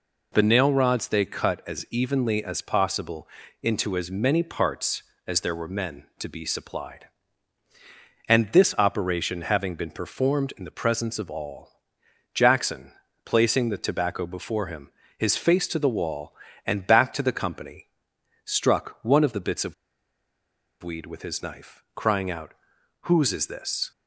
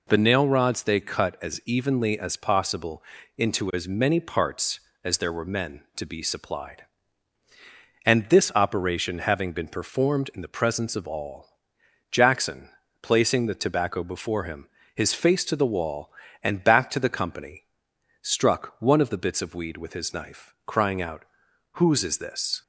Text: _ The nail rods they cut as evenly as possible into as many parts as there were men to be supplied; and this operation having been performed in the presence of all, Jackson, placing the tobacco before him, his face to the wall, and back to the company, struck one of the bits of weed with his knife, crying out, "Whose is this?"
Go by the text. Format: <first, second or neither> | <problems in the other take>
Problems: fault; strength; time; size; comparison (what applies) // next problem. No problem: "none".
second | pauses between "possible" and "into"; slight; at 3.2 s; 0.34 s long; slight in the second // pauses between "of" and "weed"; at 19.7 s; 1.0 s long